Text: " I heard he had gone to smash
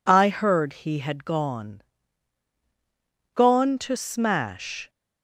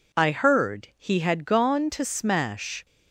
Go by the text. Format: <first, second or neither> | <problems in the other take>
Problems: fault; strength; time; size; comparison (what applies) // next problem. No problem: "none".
second | says "gone" twice; at 3.3 s